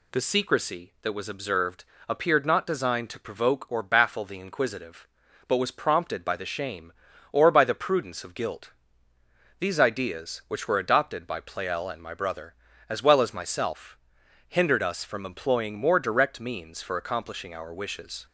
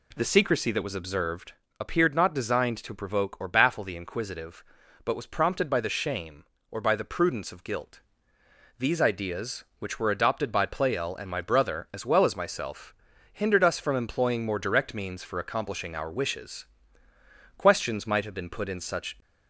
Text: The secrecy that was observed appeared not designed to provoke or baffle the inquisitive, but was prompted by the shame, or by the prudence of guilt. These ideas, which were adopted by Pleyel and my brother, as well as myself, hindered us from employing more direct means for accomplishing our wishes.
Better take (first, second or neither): first